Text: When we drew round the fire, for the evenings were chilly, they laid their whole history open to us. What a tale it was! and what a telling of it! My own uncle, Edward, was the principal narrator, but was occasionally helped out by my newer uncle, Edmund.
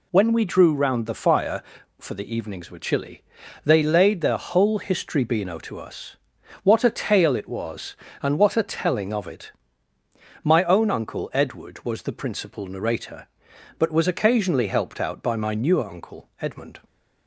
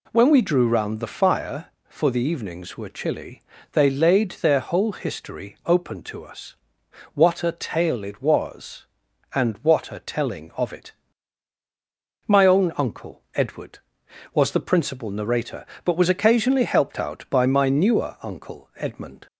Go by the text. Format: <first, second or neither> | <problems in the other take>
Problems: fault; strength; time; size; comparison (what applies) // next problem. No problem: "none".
second | says "beano" for "open"; at 5.2 s